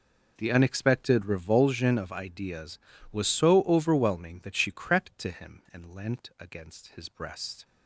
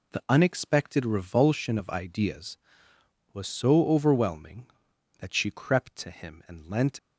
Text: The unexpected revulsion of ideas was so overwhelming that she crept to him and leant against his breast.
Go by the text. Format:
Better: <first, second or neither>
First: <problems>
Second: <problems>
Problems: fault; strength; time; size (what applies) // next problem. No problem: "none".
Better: first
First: none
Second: stops before "against his breast"; at 6.9 s